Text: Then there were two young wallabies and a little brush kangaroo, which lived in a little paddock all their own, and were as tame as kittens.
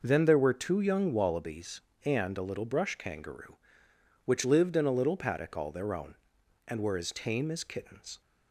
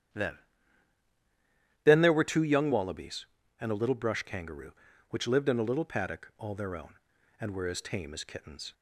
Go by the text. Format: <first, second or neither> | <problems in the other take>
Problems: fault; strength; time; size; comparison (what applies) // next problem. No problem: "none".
first | starts louder than the rest; strong; until 2.5 s; 10 dB // says "Then" twice; at 1.8 s